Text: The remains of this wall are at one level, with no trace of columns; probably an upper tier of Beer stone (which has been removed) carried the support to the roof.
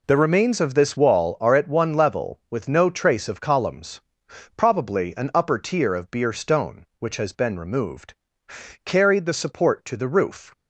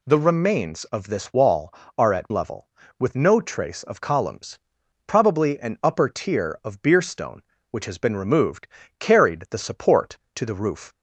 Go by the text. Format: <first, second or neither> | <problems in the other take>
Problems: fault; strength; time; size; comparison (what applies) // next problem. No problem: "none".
first | skips "one"; at 2.3 s